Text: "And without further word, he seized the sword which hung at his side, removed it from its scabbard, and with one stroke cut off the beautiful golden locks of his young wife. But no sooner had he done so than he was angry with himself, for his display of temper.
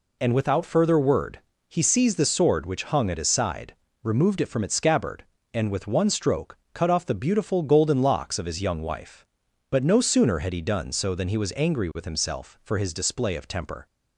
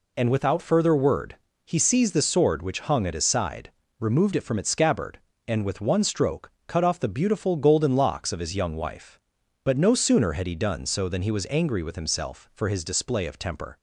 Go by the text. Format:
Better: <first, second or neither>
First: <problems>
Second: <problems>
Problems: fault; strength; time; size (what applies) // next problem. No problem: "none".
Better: neither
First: pauses between "stroke" and "cut"; slight; at 6.5 s; 0.16 s long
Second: pauses between "stroke" and "cut"; slight; at 6.5 s; 0.16 s long